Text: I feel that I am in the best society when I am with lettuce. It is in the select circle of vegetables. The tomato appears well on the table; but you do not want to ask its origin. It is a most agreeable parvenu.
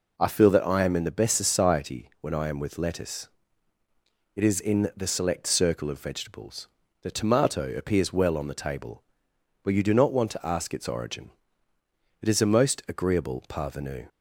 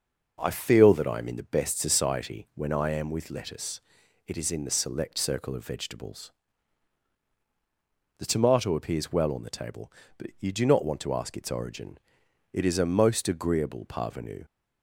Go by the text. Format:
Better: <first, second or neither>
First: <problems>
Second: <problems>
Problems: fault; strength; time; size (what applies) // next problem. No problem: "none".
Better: neither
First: none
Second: none